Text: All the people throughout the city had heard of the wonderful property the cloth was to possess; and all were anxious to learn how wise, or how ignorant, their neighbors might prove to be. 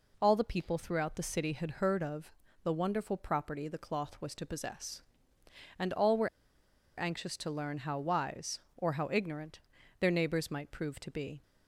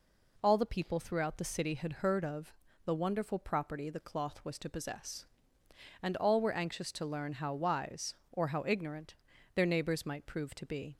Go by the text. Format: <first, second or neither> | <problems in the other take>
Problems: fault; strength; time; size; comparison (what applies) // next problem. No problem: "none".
second | pauses between "of" and "the"; slight; at 2.3 s; 0.32 s long; slight in the second // pauses between "were" and "anxious"; noticeable; at 6.2 s; 0.71 s long